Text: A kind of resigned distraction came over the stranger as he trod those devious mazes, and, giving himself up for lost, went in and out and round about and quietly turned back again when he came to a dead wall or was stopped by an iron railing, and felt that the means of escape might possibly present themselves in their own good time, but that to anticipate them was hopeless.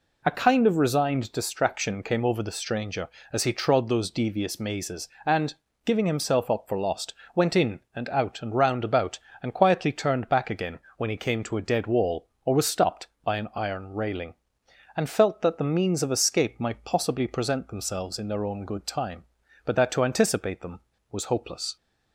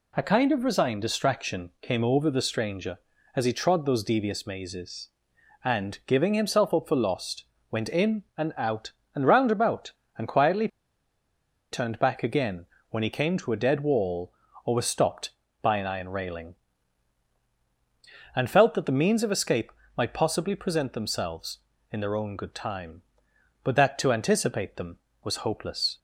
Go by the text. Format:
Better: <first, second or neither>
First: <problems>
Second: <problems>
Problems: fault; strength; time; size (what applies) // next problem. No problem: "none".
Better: first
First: pauses between "again" and "when"; slight; at 10.7 s; 0.20 s long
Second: pauses between "quietly" and "turned"; at 10.6 s; 1.0 s long // pauses between "again" and "when"; slight; at 12.6 s; 0.24 s long // pauses between "escape" and "might"; slight; at 19.7 s; 0.24 s long